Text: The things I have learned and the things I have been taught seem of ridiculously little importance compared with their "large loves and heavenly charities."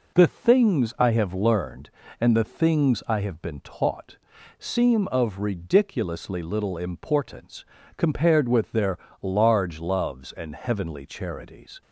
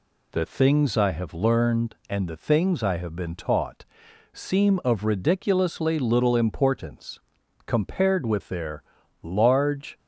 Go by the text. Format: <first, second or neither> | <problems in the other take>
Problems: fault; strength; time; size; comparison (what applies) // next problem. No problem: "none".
first | pauses between "taught" and "seem"; noticeable; at 3.8 s; 0.48 s long; also in the first // pauses between "importance" and "compared"; noticeable; at 7.1 s; 0.46 s long; slight in the first // pauses between "their" and "large"; at 8.8 s; 0.40 s long; slight in the first // stops before "loves and heavenly charities"; at 9.9 s